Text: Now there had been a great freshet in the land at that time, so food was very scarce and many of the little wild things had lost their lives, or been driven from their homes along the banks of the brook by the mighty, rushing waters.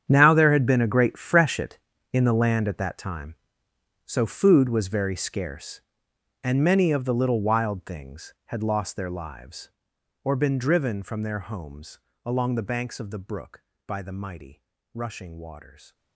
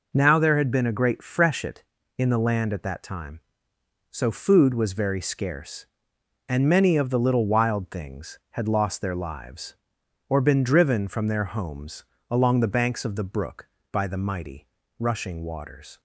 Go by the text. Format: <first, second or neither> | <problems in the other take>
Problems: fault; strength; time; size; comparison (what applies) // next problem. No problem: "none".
second | gets quieter; strong; throughout; 16.5 dB // pauses between "homes" and "along"; slight; at 11.9 s; 0.24 s long; slight in the second